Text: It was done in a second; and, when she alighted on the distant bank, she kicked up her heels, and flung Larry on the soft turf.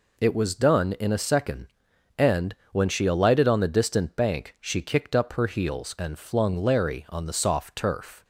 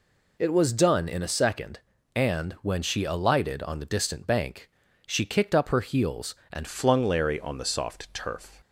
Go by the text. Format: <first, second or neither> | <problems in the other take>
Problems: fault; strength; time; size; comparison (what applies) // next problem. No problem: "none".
first | changes voice at "flung"; from 6.6 s on; 2.0 s long